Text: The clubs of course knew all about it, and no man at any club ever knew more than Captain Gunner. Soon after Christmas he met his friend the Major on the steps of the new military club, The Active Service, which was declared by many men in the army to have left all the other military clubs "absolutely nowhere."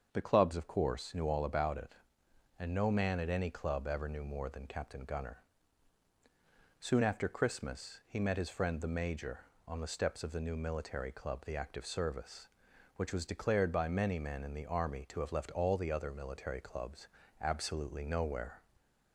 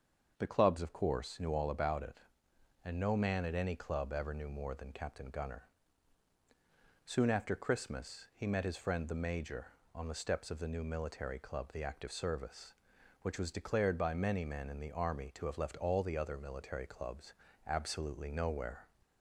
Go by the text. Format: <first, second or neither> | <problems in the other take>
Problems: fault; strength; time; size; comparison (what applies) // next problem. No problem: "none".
neither | starts louder than the rest; the same in both // pauses between "clubs" and "absolutely"; slight; the same in both